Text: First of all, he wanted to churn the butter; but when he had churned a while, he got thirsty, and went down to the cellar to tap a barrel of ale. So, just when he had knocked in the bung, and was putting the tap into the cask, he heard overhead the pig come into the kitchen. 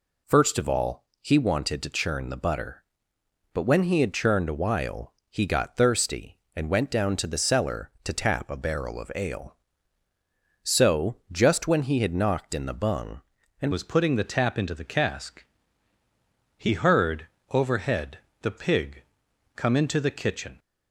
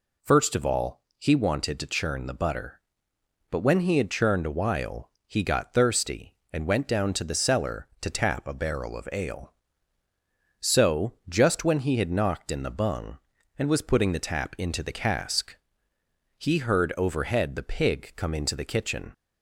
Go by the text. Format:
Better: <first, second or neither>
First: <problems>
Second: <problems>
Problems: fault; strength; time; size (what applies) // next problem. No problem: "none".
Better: second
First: changes voice at "was"; from 13.7 s on; 6.8 s long // pauses between "heard" and "overhead"; slight; at 17.2 s; 0.22 s long // pauses between "overhead" and "the"; slight; at 18.1 s; 0.22 s long // pauses between "pig" and "come"; noticeable; at 19.0 s; 0.52 s long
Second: none